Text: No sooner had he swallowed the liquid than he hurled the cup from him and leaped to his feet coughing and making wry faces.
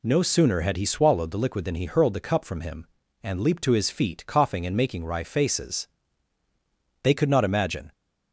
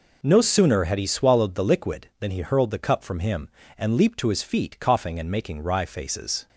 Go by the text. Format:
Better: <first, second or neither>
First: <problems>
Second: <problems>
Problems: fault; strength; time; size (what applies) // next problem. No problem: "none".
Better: second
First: goes on to say "They could not imagine"; noticeable; from 7.0 s on; 0.90 s long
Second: none